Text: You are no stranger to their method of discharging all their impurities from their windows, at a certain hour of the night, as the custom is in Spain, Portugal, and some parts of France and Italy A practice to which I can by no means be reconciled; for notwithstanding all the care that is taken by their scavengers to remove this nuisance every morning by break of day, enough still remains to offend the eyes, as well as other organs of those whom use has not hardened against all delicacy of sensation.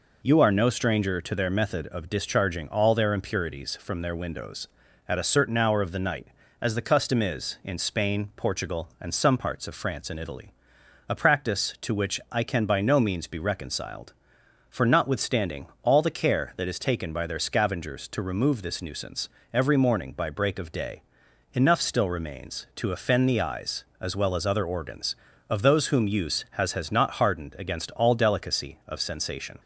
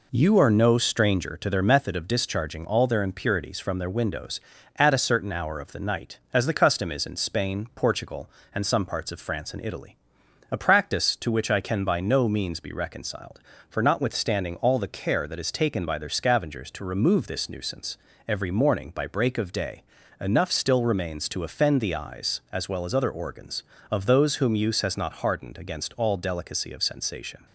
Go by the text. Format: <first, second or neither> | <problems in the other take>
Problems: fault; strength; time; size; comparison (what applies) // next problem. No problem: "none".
second | pauses between "Italy" and "A"; noticeable; at 10.5 s; 0.54 s long; noticeable in the second // pauses between "notwithstanding" and "all"; slight; at 15.6 s; 0.16 s long // pauses between "nuisance" and "every"; slight; at 19.2 s; 0.26 s long; slight in the second // says "has" twice; at 26.7 s